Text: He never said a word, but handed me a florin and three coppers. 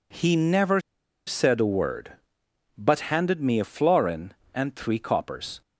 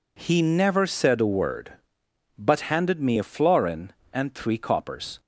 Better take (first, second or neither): second